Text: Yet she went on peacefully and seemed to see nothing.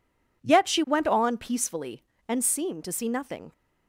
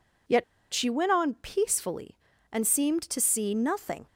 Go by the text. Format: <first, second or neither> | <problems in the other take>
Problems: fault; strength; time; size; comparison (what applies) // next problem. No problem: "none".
first | pauses between "Yet" and "she"; slight; at 0.4 s; 0.28 s long